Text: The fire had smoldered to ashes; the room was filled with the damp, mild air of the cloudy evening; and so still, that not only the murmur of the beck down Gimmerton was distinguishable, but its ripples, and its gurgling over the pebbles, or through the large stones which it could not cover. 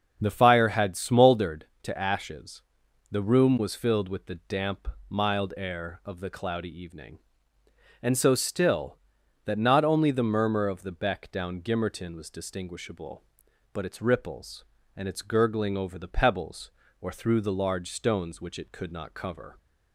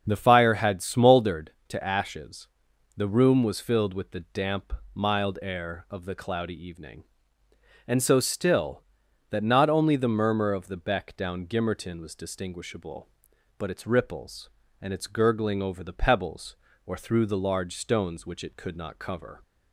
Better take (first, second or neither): neither